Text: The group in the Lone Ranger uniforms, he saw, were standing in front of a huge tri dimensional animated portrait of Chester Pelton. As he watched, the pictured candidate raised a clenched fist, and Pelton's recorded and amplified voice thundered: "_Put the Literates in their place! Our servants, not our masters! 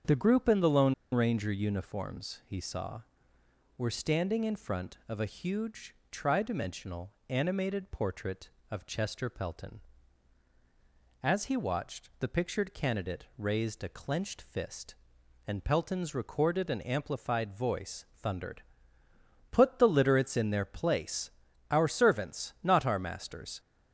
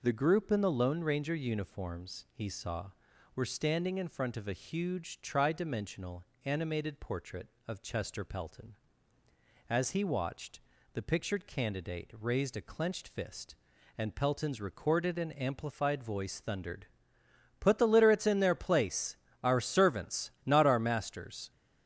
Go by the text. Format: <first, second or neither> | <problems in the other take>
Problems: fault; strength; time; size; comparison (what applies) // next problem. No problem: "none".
second | starts louder than the rest; strong; until 1.2 s; 7.5 dB // pauses between "Lone" and "Ranger"; slight; at 0.9 s; 0.19 s long // pauses between "huge" and "tri"; slight; at 5.9 s; 0.18 s long // pauses between "dimensional" and "animated"; slight; at 7.1 s; 0.16 s long; slight in the second